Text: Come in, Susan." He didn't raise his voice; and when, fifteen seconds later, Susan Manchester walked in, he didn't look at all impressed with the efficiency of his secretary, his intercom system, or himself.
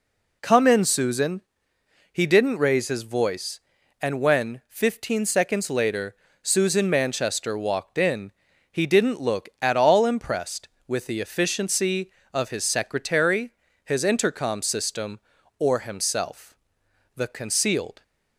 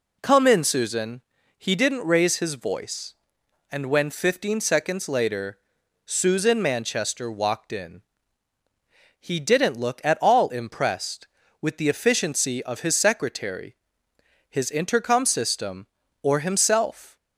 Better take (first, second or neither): second